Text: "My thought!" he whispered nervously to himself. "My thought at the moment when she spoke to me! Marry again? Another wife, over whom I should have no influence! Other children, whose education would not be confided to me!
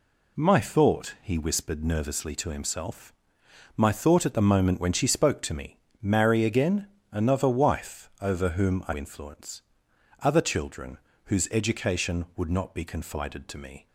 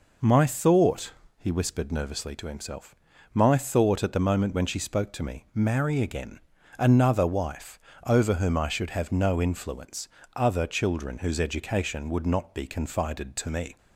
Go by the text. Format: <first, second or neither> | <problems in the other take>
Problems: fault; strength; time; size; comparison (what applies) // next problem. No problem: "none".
second | skips "should have no"; at 8.9 s